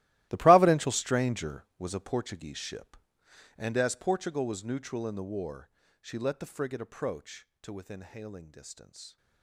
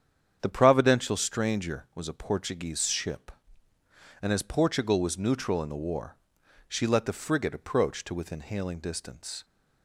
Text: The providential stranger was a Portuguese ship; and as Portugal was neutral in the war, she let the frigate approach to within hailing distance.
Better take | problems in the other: second | gets quieter; strong; throughout; 16.5 dB // starts louder than the rest; strong; until 1.3 s; 16 dB; strong in the second

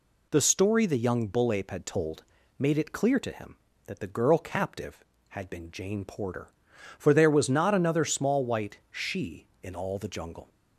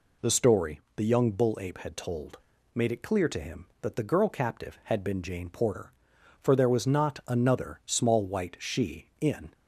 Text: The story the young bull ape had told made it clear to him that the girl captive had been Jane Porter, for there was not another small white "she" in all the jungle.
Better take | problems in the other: first | pauses between "story" and "the"; slight; at 0.8 s; 0.16 s long // pauses between "told" and "made"; slight; at 2.3 s; 0.36 s long; slight in the first // stops before "all the jungle"; at 9.5 s

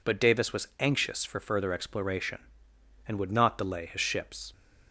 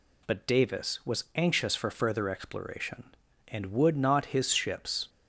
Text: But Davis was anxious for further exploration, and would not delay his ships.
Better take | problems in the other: first | skips "delay"; at 4.2 s

